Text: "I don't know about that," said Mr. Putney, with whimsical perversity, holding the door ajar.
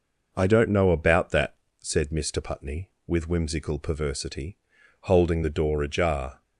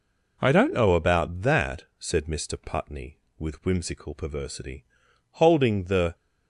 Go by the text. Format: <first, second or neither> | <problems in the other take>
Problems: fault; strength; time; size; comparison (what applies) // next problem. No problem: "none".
first | stops before "door ajar"; at 6.1 s